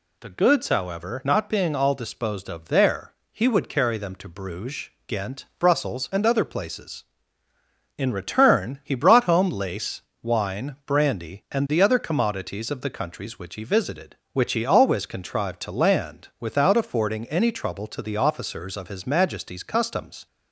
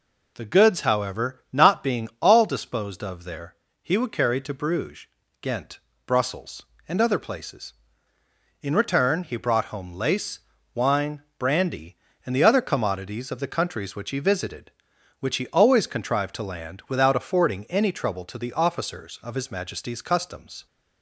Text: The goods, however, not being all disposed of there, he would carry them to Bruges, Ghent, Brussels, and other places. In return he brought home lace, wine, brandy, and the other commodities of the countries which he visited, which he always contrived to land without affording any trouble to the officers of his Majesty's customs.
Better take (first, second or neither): first